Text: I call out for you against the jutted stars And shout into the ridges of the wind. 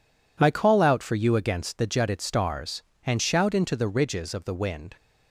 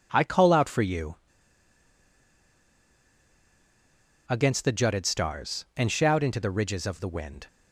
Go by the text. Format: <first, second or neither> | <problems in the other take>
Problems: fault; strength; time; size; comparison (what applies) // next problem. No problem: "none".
first | pauses between "you" and "against"; strong; at 1.1 s; 3.1 s long